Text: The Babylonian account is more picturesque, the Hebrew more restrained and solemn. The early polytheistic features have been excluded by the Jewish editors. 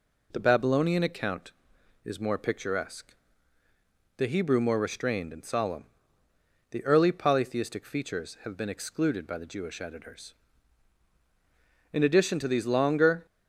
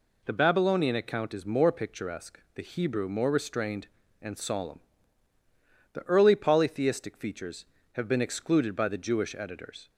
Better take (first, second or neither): second